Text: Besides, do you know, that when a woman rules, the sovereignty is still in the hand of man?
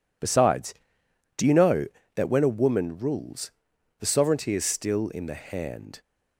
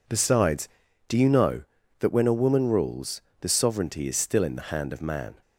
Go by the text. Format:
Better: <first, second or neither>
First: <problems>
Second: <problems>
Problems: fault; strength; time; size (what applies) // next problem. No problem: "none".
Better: second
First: stops before "of man"; at 6.0 s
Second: none